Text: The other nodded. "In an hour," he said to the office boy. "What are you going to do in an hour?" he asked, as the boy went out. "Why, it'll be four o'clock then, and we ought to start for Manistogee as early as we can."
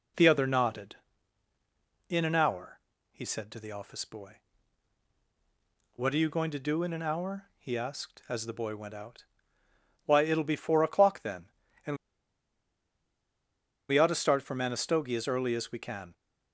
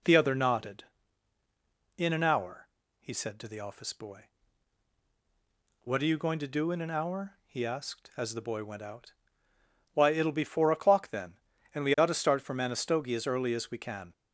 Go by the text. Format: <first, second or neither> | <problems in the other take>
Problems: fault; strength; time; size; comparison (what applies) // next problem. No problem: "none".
second | pauses between "and" and "we"; strong; at 11.9 s; 1.9 s long